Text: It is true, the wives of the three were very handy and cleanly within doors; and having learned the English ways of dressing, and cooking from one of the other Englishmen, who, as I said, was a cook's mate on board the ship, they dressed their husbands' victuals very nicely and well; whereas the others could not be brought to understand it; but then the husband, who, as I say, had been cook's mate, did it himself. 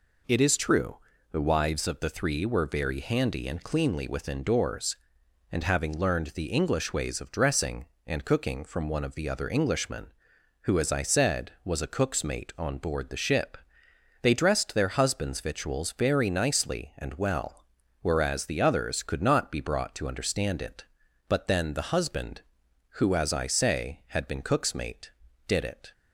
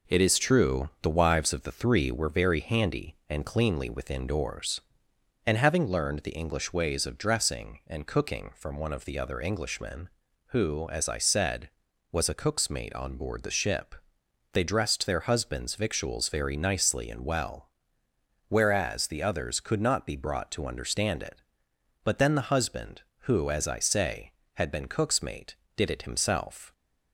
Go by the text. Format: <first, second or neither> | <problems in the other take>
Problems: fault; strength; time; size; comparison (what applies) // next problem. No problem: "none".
second | stops before "himself"; at 25.9 s